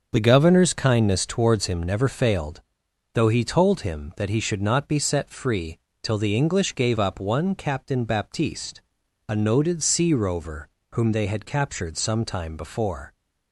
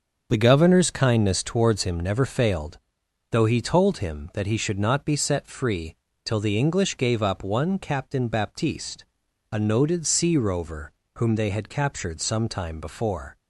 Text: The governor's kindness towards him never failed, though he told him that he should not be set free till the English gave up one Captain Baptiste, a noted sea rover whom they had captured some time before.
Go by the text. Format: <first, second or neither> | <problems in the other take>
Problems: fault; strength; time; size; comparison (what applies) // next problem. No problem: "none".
neither | starts louder than the rest; the same in both // pauses between "free" and "till"; slight; the same in both // pauses between "rover" and "whom"; slight; the same in both